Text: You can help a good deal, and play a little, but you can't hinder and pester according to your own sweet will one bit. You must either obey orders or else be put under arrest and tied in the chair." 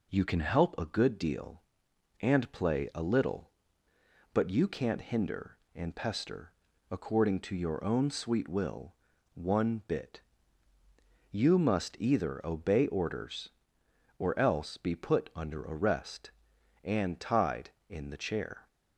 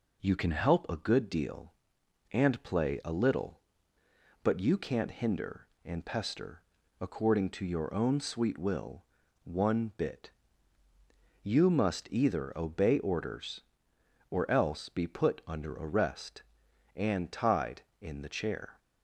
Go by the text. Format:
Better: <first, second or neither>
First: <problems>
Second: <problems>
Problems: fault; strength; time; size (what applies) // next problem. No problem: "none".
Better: neither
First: pauses between "pester" and "according"; at 6.5 s; 0.38 s long // pauses between "will" and "one"; at 8.9 s; 0.40 s long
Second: pauses between "pester" and "according"; at 6.6 s; 0.38 s long // pauses between "will" and "one"; at 9.0 s; 0.40 s long